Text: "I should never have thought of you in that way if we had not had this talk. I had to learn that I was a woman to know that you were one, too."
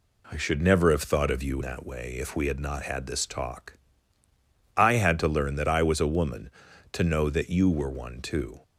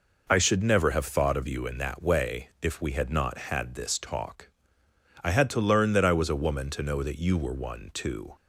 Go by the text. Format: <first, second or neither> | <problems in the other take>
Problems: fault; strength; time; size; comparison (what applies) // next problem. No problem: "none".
second | skips "in"; at 1.6 s